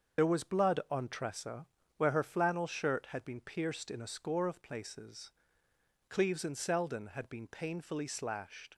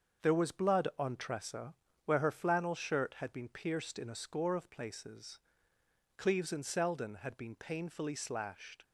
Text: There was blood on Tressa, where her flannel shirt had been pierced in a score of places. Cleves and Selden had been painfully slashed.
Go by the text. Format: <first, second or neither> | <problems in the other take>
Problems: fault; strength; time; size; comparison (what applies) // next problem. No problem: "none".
second | loses the start of "There"; at 0.1 s; 45 ms // starts louder than the rest; until 1.2 s; 6.5 dB; also in the second